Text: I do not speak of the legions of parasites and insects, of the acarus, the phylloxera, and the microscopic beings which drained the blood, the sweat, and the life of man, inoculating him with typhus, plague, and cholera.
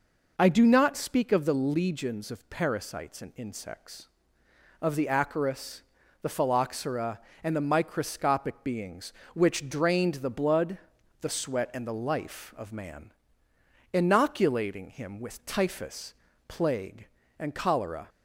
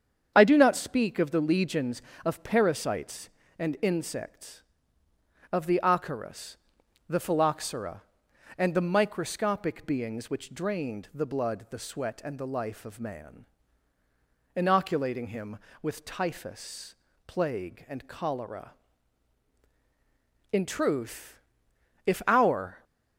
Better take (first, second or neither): first